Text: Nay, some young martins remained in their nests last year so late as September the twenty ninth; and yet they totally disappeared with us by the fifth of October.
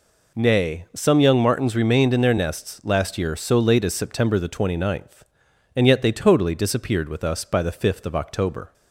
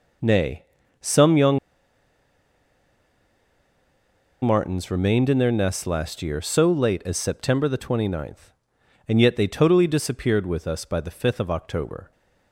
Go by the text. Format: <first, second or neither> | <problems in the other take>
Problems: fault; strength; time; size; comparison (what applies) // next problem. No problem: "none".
first | pauses between "young" and "martins"; strong; at 1.5 s; 2.8 s long